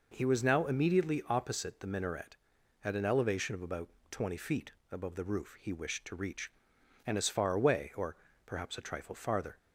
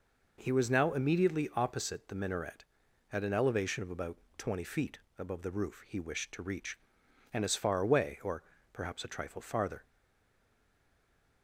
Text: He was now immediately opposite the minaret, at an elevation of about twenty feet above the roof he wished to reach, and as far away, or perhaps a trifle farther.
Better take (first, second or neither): first